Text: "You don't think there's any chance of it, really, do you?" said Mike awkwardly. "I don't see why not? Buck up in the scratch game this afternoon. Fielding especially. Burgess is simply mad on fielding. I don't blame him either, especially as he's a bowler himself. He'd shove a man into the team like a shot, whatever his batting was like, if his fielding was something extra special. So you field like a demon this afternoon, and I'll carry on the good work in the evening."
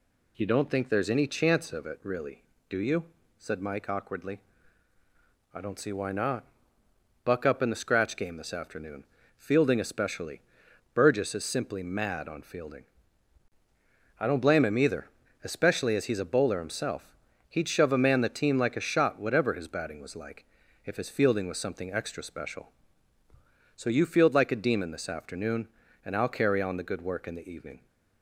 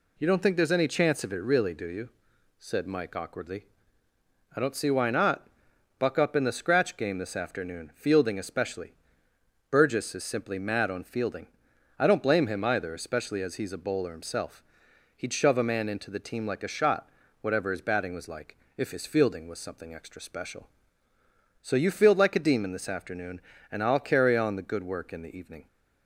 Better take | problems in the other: second | skips "into"; at 18.2 s

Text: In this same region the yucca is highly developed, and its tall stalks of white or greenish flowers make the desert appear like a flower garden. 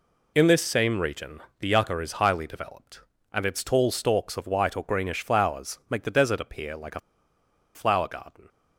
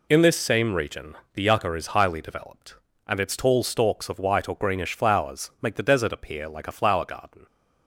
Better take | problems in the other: second | pauses between "region" and "the"; slight; at 1.4 s; 0.18 s long; slight in the second // pauses between "a" and "flower"; noticeable; at 6.9 s; 0.75 s long

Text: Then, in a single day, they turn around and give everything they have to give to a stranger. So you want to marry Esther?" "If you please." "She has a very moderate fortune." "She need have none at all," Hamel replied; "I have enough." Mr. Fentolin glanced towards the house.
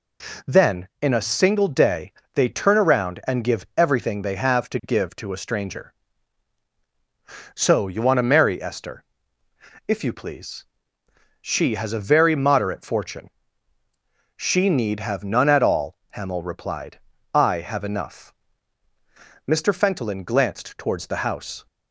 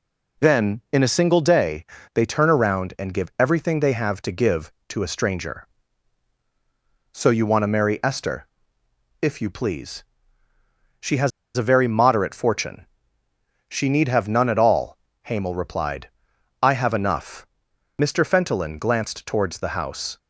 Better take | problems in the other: first | pauses between "has" and "a"; slight; at 11.3 s; 0.27 s long

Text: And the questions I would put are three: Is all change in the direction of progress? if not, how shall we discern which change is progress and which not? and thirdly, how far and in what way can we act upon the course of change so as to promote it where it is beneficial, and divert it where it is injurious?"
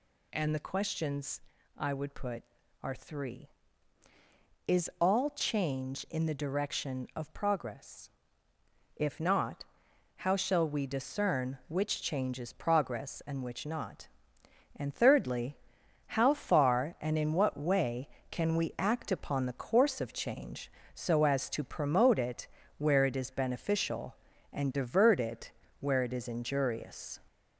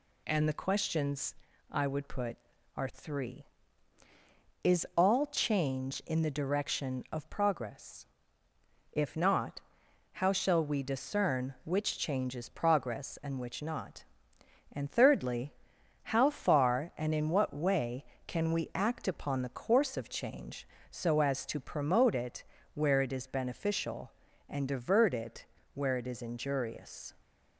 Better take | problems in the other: second | gets louder; slight; throughout; 3 dB // pauses between "questions" and "I"; slight; at 1.4 s; 0.36 s long; slight in the second // pauses between "it" and "where"; slight; at 22.4 s; 0.30 s long; slight in the second // pauses between "it" and "where"; slight; at 25.5 s; 0.30 s long; slight in the second

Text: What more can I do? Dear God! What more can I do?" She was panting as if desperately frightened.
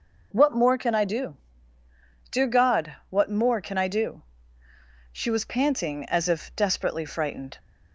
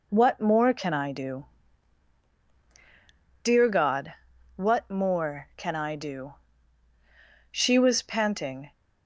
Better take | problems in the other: first | stops before "as if desperately frightened"; at 8.7 s

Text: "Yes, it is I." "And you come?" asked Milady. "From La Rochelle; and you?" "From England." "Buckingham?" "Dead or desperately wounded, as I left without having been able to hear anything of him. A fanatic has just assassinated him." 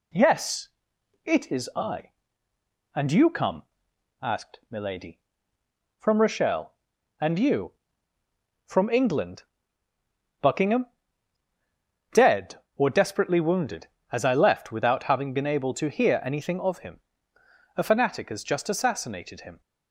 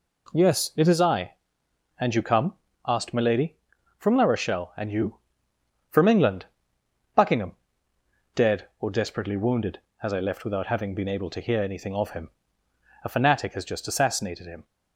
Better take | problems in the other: second | skips "La"; at 6.2 s

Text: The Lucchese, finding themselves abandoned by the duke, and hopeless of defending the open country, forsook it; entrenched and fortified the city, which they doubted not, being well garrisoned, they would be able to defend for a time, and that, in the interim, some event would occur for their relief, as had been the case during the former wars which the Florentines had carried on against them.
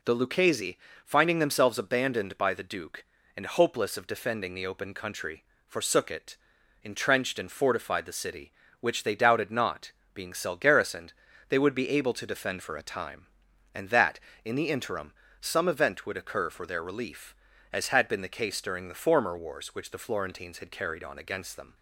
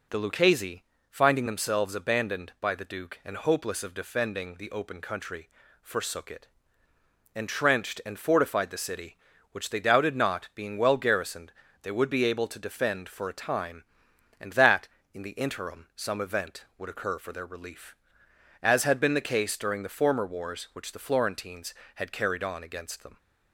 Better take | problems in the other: second | says "cell" for "well"; at 10.3 s

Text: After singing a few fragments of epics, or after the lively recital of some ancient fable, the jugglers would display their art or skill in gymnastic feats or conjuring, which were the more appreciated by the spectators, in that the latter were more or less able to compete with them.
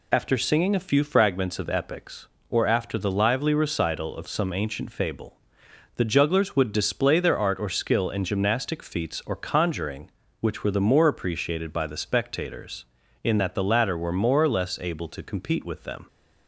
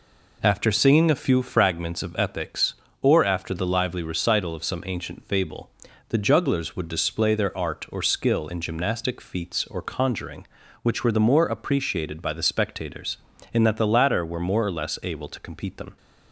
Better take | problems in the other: first | skips "with"; at 15.7 s

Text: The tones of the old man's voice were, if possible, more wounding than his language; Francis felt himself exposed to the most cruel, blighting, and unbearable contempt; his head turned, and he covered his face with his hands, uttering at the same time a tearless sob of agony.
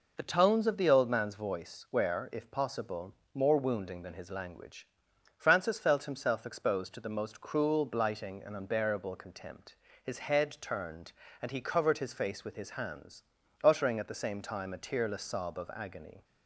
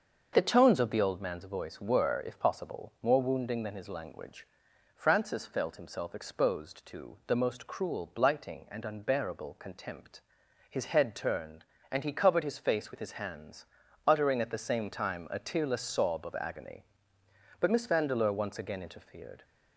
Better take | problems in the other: first | starts louder than the rest; until 1.3 s; 6.5 dB // goes on to say "But Miss Vandeleur once again interfered"; strong; from 17.5 s on; 1.8 s long

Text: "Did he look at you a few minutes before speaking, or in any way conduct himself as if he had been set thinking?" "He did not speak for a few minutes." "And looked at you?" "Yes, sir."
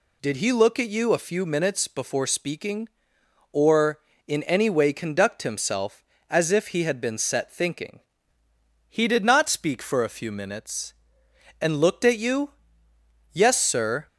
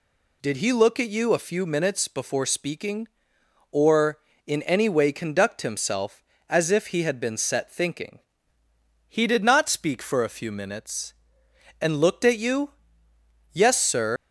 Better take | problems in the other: first | leaves "sir" unfinished; at 14.1 s; 105 ms

